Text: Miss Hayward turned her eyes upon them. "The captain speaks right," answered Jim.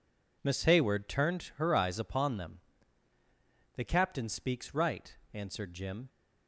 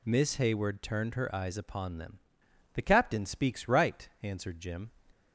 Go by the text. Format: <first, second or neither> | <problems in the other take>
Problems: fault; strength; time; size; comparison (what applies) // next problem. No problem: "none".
neither | none